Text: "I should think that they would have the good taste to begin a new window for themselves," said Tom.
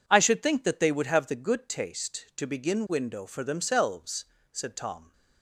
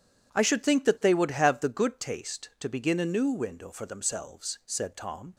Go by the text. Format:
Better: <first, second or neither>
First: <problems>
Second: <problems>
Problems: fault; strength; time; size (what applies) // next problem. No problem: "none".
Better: second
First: skips "a new"; at 2.8 s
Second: none